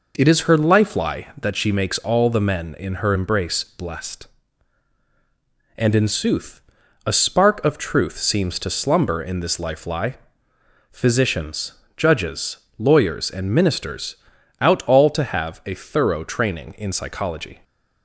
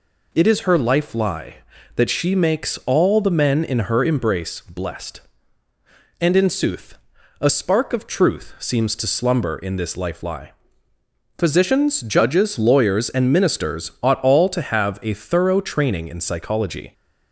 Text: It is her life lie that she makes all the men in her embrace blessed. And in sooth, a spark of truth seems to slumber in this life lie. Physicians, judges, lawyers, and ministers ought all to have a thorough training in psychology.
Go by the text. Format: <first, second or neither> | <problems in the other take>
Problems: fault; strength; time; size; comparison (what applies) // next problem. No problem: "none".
second | says "out" for "ought"; at 14.6 s